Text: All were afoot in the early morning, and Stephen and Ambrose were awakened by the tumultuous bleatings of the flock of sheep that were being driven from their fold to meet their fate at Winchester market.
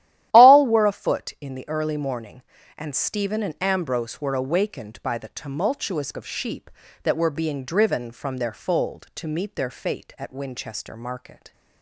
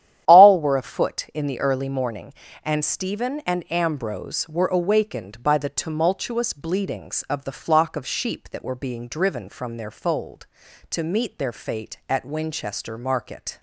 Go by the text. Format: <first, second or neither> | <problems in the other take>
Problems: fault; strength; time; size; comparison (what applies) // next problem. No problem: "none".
second | starts louder than the rest; strong; until 1.3 s; 13 dB; strong in the second // skips "bleatings of the flock"; at 6.1 s